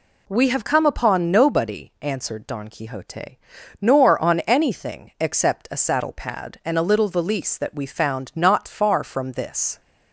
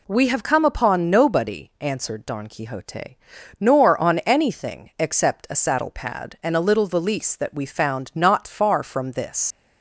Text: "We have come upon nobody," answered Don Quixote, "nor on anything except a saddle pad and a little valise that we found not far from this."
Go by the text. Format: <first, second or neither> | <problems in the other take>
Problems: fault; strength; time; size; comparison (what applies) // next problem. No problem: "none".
first | leaves "this" unfinished; at 9.5 s; 90 ms